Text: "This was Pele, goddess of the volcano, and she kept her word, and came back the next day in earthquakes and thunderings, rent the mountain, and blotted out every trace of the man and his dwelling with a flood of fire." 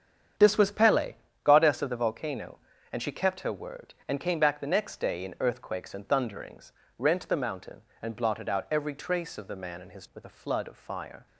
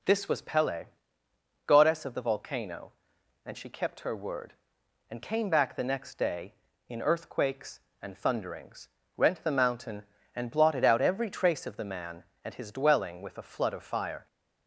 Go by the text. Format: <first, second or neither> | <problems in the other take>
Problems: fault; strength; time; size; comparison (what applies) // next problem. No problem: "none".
second | starts louder than the rest; strong; until 1.6 s; 8.5 dB // skips "dwelling"; at 10.1 s